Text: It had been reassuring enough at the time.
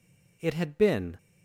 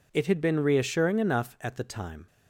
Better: second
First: stops before "reassuring enough at the time"; at 1.1 s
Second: none

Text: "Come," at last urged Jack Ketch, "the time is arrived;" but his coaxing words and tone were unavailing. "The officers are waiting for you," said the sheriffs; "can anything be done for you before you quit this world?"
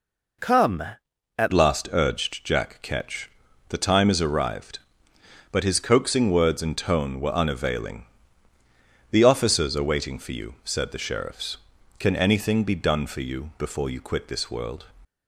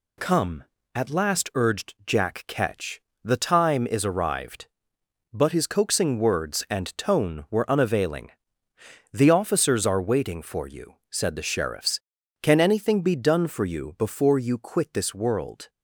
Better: second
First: changes voice at "last"; from 1.5 s on; 13.3 s long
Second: none

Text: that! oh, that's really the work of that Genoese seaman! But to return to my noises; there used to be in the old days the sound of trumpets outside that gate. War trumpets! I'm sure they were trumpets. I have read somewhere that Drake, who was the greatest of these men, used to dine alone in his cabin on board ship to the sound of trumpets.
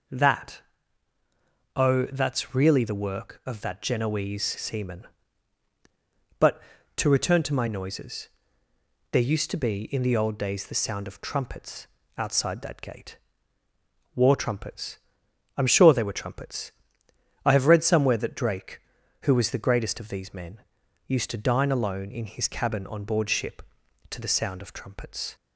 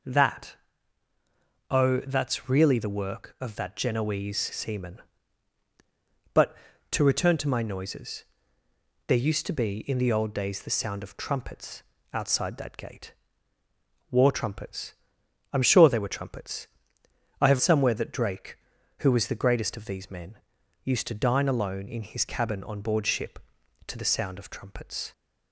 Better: first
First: pauses between "trumpets" and "outside"; slight; at 11.8 s; 0.30 s long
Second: pauses between "trumpets" and "outside"; slight; at 11.8 s; 0.30 s long // skips "read"; at 17.5 s

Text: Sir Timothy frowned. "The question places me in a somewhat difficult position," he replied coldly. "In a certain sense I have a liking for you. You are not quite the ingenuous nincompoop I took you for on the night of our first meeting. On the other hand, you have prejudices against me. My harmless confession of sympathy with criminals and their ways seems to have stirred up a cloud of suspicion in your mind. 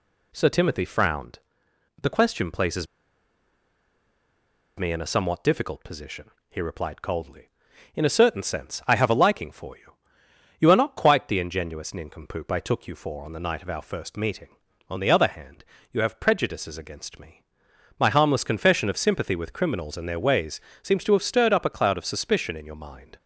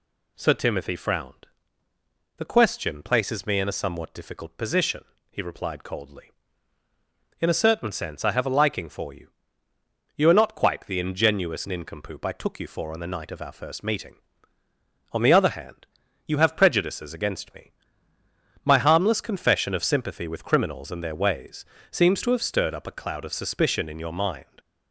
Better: second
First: pauses between "places" and "me"; strong; at 2.8 s; 1.9 s long // pauses between "ways" and "seems"; slight; at 20.6 s; 0.24 s long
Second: pauses between "ways" and "seems"; slight; at 21.6 s; 0.24 s long

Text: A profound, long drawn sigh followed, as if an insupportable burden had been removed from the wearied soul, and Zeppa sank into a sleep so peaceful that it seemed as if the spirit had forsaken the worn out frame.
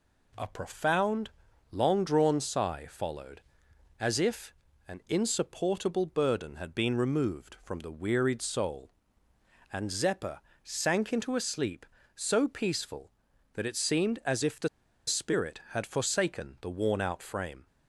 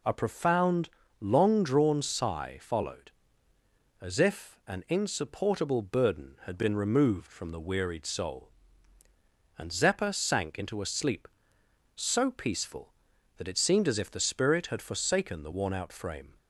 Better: second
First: pauses between "if" and "an"; slight; at 4.5 s; 0.36 s long // pauses between "Zeppa" and "sank"; slight; at 10.3 s; 0.24 s long // pauses between "the" and "spirit"; at 14.6 s; 0.39 s long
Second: none

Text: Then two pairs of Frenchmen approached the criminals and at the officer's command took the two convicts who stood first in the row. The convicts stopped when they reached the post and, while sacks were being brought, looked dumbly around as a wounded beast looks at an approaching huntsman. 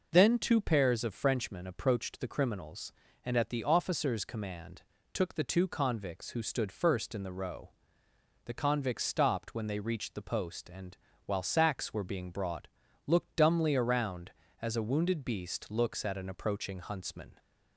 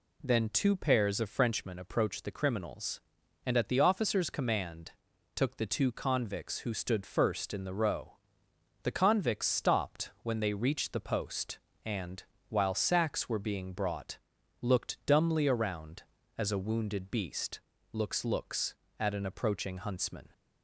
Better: first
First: pauses between "command" and "took"; slight; at 4.8 s; 0.28 s long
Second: pauses between "command" and "took"; at 4.9 s; 0.42 s long // pauses between "beast" and "looks"; slight; at 17.5 s; 0.34 s long // says "looks" twice; at 18.2 s

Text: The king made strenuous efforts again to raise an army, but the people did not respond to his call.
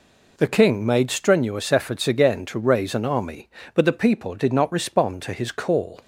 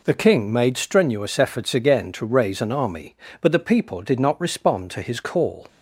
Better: neither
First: none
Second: none

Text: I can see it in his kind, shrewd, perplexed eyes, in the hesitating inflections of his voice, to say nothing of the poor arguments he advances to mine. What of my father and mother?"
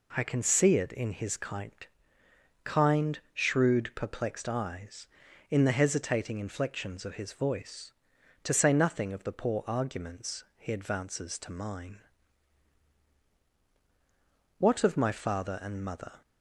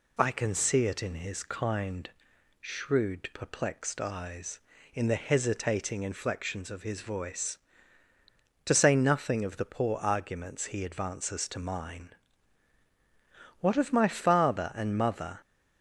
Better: second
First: says "kind" twice; at 2.6 s // pauses between "arguments" and "he"; slight; at 10.4 s; 0.16 s long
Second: none

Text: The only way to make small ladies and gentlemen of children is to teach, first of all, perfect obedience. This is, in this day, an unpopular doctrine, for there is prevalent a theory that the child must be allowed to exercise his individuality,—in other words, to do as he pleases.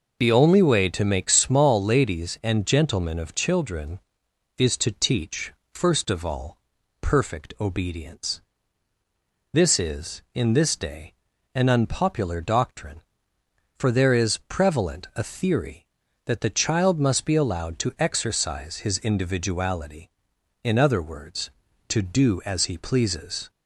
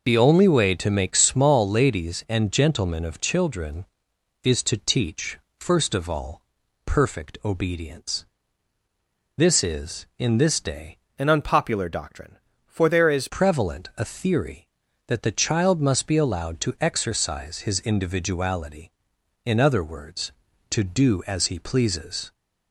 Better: first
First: none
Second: changes voice from "an" to "is"; from 11.1 to 13.2 s; 2.1 s long

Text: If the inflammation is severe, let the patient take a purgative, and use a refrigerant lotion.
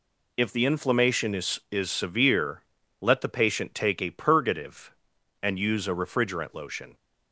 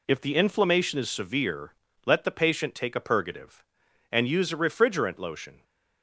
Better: second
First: says "is" twice; at 1.6 s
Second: none

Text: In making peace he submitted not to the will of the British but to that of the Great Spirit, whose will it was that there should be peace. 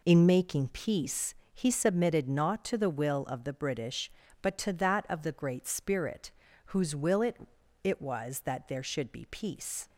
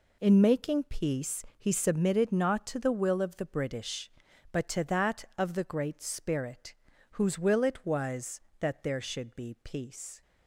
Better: second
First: pauses between "peace" and "he"; slight; at 1.3 s; 0.18 s long // says "it" twice; at 7.8 s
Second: none

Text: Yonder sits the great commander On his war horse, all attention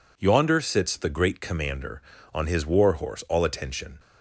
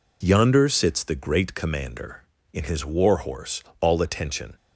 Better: first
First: none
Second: says "In" for "On"; at 2.5 s

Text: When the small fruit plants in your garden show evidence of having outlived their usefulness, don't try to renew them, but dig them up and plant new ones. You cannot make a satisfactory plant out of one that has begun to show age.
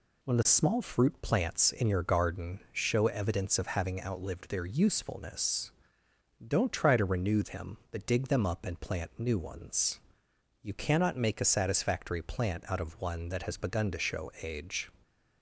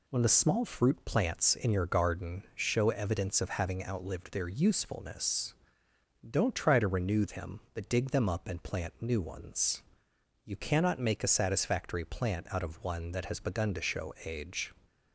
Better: neither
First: none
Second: none

